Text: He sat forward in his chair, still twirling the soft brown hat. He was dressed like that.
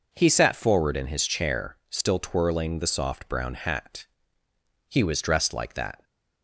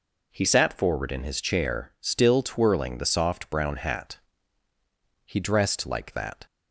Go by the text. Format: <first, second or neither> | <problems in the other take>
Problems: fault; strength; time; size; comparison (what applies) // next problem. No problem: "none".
first | skips "was"; at 5.4 s